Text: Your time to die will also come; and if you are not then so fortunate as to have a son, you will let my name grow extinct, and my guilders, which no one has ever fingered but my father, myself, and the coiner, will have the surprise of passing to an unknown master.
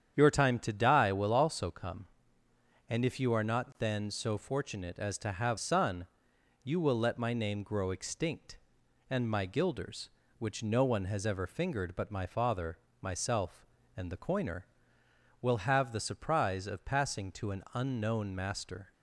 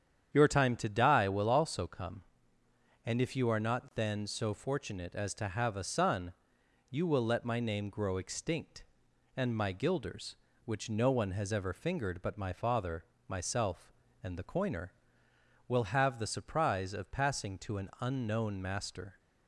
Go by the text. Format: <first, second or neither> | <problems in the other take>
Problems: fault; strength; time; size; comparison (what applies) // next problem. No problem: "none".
second | starts louder than the rest; strong; until 1.1 s; 8.5 dB; strong in the second // skips "a"; at 5.5 s